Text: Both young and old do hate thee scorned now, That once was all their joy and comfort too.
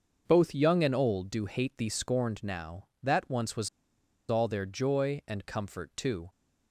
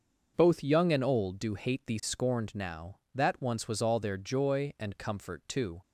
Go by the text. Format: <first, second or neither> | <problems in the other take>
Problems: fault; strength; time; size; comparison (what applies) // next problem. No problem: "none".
second | starts louder than the rest; until 1.2 s; 6.5 dB; also in the second // pauses between "was" and "all"; noticeable; at 3.6 s; 0.61 s long